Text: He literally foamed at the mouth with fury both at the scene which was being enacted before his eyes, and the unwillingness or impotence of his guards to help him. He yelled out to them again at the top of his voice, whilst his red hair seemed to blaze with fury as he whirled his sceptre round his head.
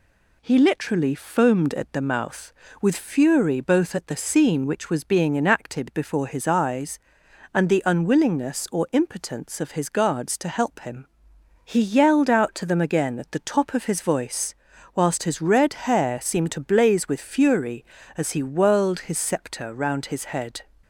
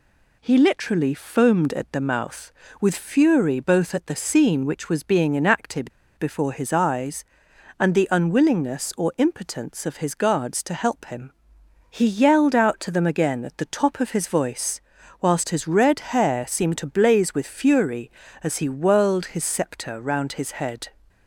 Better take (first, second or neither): first